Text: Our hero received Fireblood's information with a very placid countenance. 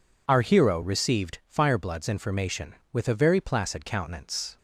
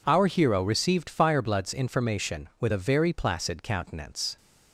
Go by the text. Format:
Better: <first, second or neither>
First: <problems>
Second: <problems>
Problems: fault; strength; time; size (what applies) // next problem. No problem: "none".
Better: neither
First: none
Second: none